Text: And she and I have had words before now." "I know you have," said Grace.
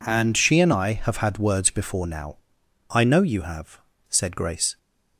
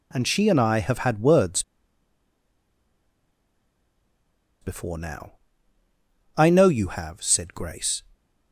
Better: first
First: none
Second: pauses between "words" and "before"; strong; at 1.6 s; 2.9 s long

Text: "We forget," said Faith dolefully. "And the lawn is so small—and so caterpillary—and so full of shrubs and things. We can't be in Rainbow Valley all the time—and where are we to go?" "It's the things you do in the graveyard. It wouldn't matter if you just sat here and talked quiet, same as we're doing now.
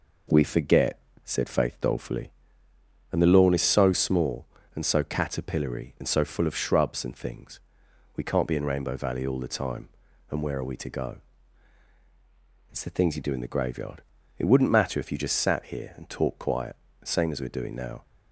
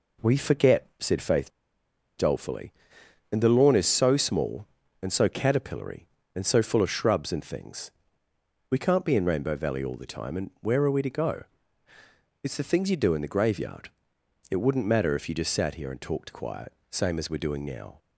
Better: first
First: none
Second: pauses between "Faith" and "dolefully"; noticeable; at 1.4 s; 0.68 s long

